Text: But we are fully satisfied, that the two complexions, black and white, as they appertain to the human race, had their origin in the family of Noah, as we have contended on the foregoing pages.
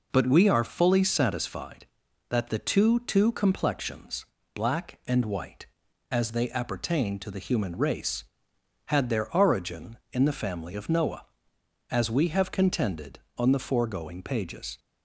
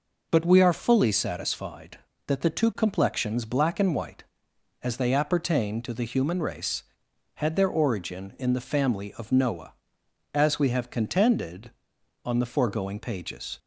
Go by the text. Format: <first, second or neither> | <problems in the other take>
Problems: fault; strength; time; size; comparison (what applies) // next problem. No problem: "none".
second | says "two" twice; at 3.0 s